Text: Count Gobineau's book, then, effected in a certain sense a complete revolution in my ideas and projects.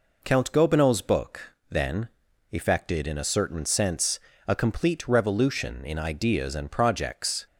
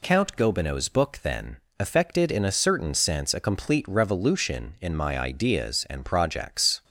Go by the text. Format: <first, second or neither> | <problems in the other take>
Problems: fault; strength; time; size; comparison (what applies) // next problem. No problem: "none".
second | pauses between "sense" and "a"; slight; at 4.1 s; 0.26 s long // skips "my"; at 5.9 s